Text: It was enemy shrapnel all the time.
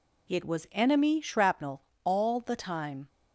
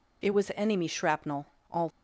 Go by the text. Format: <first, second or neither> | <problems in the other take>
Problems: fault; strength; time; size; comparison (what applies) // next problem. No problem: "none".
first | pauses between "shrapnel" and "all"; slight; at 1.4 s; 0.24 s long; slight in the first // stops before "the time"; at 1.9 s